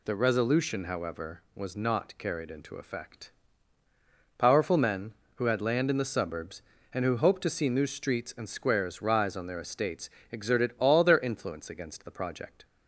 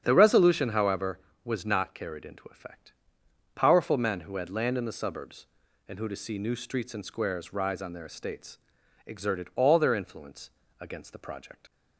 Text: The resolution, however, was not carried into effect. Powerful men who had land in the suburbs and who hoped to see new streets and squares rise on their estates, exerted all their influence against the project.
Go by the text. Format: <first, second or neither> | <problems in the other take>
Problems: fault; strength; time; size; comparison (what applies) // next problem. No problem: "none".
first | starts louder than the rest; strong; until 1.0 s; 8 dB // skips "hoped"; at 6.0 s // pauses between "influence" and "against"; slight; at 10.4 s; 0.28 s long